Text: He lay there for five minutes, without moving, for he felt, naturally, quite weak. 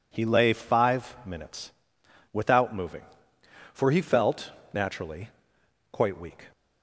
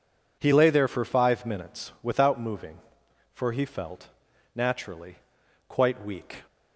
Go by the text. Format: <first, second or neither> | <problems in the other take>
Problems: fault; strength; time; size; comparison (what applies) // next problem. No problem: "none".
second | skips "there for"; at 0.5 s